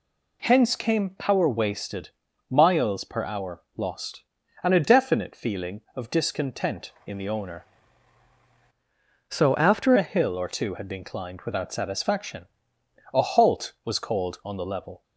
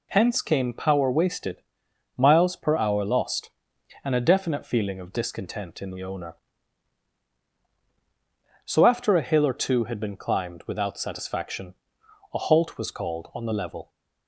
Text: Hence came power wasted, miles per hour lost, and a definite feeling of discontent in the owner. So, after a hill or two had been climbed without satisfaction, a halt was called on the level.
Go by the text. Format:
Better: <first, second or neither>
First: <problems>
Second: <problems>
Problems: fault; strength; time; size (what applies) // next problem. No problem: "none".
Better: second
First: pauses between "hour" and "lost"; slight; at 3.6 s; 0.16 s long // changes voice from "So" to "after"; from 9.3 to 9.9 s; 0.6 s long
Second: none